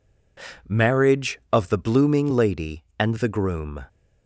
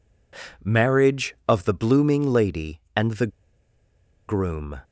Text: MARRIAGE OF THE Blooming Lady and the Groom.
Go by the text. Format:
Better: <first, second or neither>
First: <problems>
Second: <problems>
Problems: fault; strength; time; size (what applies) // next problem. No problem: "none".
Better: first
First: none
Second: pauses between "the" and "Groom"; at 3.2 s; 1.0 s long